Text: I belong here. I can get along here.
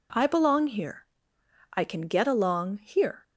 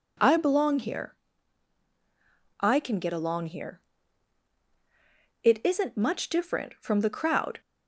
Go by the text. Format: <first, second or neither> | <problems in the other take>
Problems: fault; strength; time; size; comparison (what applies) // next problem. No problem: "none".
first | goes on to say "It isn't much different from the crowd"; strong; from 5.4 s on; 2.1 s long